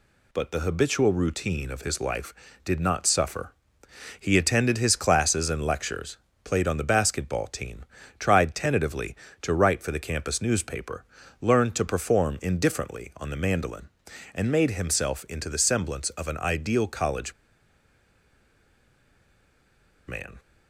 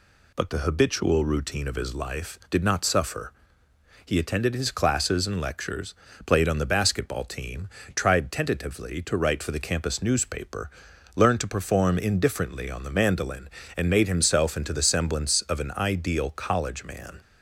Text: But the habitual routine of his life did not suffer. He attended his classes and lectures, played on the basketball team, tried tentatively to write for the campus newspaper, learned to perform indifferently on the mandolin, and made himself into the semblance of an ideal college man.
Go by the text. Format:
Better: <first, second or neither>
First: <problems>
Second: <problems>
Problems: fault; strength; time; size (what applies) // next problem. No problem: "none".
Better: second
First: pauses between "college" and "man"; strong; at 17.3 s; 2.7 s long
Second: none